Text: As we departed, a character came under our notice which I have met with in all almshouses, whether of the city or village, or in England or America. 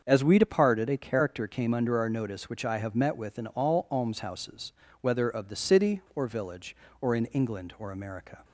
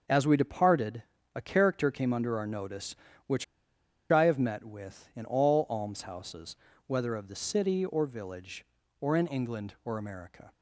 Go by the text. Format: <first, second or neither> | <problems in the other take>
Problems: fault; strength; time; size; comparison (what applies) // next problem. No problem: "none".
first | starts louder than the rest; until 1.3 s; 6.5 dB; also in the first // pauses between "which" and "I"; noticeable; at 3.4 s; 0.66 s long